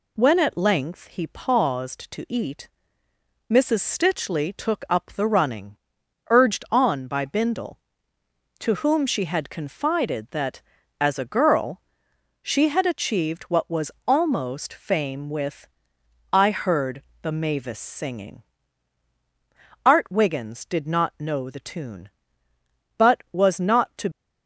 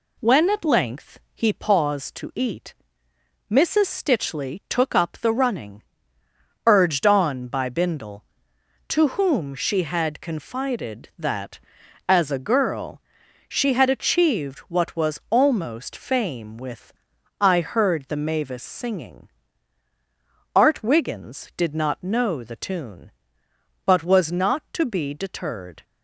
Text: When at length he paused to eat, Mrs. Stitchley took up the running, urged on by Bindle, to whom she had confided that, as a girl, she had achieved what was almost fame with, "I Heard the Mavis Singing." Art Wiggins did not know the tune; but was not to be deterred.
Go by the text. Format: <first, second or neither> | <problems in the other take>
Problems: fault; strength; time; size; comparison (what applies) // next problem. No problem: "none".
second | pauses between "was" and "almost"; slight; at 13.9 s; 0.16 s long // pauses between "Heard" and "the"; slight; at 17.0 s; 0.18 s long // stops before "be deterred"; at 24.1 s